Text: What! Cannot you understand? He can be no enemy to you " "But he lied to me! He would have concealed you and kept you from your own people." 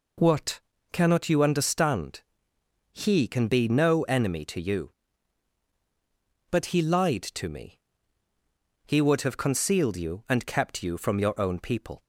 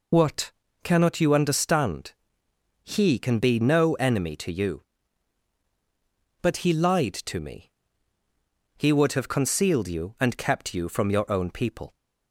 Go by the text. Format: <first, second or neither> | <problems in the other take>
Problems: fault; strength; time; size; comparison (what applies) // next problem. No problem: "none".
first | loses the start of "What"; at 0.1 s; 35 ms